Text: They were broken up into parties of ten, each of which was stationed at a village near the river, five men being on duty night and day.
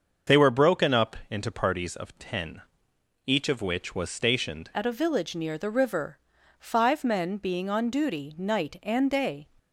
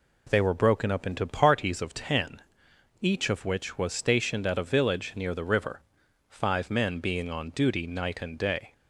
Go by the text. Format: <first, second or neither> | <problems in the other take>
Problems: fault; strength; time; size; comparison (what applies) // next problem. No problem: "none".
second | starts louder than the rest; until 1.4 s; 6.5 dB // changes voice at "at"; from 4.7 s on; 4.7 s long